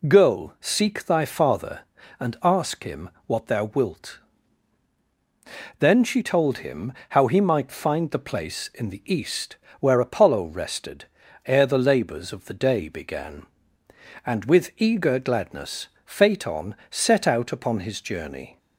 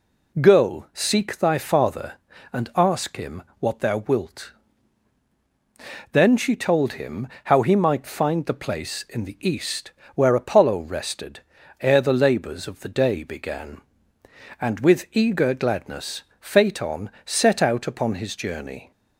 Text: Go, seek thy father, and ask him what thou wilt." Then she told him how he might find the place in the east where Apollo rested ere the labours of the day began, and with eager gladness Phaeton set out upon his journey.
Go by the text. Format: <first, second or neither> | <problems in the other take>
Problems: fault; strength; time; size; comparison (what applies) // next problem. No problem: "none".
neither | pauses between "him" and "what"; slight; the same in both // pauses between "him" and "how"; slight; the same in both // pauses between "east" and "where"; slight; the same in both // pauses between "rested" and "ere"; the same in both // pauses between "gladness" and "Phaeton"; slight; the same in both